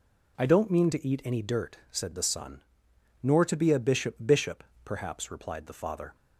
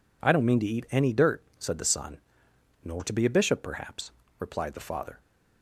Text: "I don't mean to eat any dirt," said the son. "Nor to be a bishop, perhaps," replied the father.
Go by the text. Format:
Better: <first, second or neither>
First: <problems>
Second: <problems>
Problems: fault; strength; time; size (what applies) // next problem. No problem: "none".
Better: second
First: says "bishop" twice; at 4.2 s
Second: none